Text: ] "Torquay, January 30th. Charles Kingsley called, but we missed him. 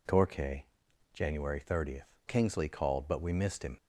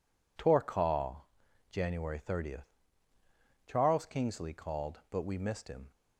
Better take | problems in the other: second | skips "Charles"; at 2.1 s

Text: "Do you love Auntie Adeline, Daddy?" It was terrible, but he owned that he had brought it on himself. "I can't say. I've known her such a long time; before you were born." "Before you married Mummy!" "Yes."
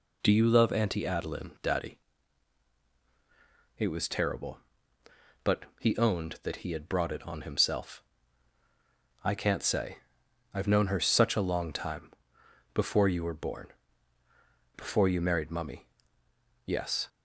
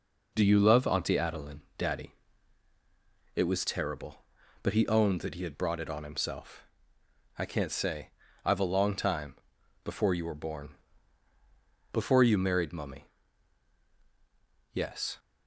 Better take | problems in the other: first | skips "known her such"; at 8.6 s

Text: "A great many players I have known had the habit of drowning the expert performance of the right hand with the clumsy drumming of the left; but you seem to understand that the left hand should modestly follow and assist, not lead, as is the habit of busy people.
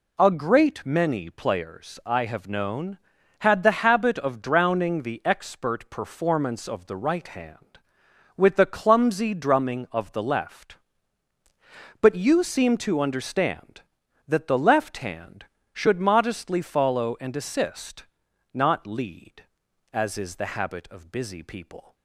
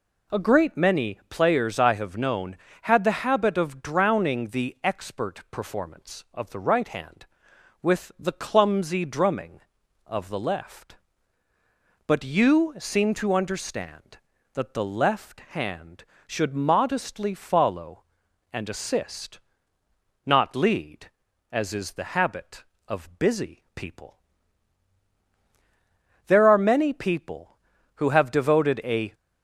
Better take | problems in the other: first | goes on to say "There are many people who have devoted a"; strong; from 26.2 s on; 2.8 s long

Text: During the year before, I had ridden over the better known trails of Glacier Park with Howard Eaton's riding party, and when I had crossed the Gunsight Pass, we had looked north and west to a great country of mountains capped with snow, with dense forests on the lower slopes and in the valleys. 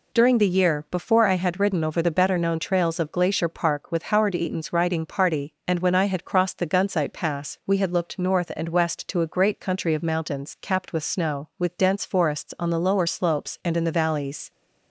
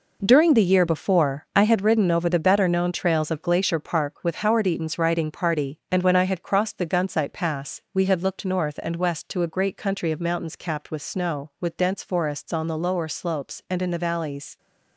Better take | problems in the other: first | gets quieter; strong; throughout; 10 dB

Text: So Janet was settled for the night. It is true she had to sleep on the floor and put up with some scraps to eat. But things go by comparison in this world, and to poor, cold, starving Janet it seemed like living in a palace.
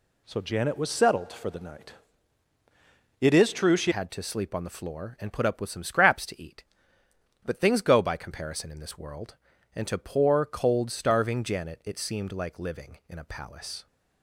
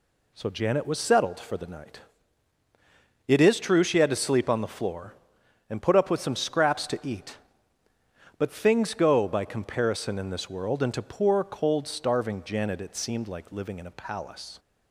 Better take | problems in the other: second | changes voice at "had"; from 3.9 s on; 9.9 s long

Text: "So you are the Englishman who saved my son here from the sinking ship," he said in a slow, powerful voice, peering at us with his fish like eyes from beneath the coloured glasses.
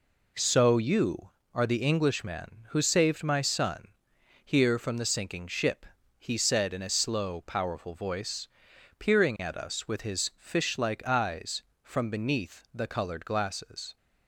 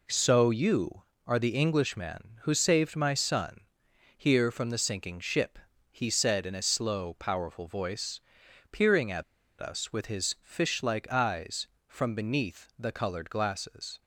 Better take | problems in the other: first | pauses between "son" and "here"; noticeable; at 3.5 s; 0.56 s long; noticeable in the first // pauses between "at" and "us"; at 9.2 s; 0.37 s long

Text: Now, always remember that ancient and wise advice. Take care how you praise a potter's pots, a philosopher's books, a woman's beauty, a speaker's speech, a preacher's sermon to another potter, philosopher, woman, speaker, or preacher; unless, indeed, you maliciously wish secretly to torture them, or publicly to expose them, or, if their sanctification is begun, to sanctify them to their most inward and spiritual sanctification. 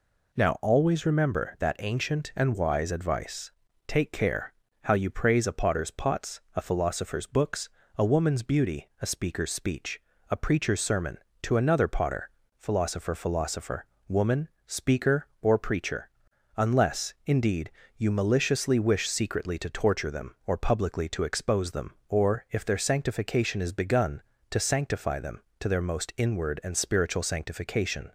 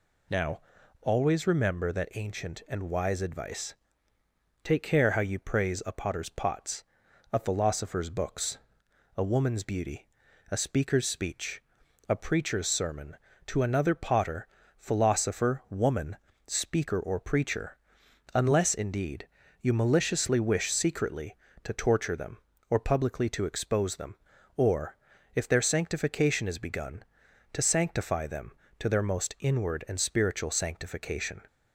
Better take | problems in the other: second | pauses between "care" and "how"; slight; at 4.5 s; 0.28 s long // says "philosopher" twice; at 13.1 s

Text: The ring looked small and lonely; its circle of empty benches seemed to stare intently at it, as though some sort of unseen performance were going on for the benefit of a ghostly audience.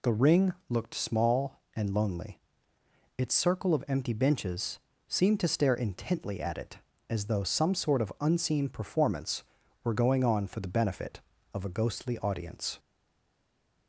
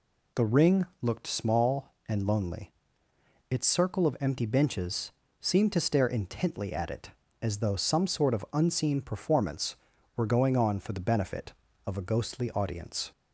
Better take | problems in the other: second | pauses between "benches" and "seemed"; slight; at 4.7 s; 0.28 s long; slight in the second // stays silent after the last word; from 12.7 s on; 1.1 s long

